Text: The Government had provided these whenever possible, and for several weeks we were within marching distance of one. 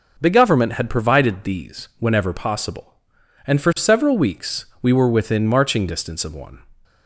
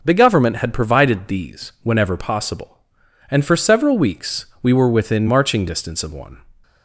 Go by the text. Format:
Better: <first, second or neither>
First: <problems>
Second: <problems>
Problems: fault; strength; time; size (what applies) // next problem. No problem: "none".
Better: neither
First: none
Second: none